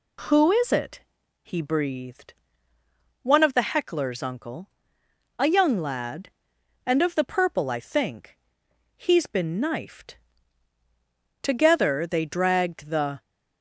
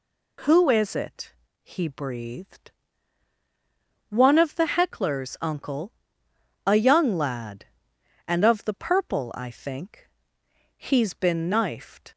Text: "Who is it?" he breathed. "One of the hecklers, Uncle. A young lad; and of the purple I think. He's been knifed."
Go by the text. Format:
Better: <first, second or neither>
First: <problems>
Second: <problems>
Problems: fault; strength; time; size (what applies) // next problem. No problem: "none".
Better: second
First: goes on to say "Together they dragged the"; strong; from 11.4 s on; 1.8 s long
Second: none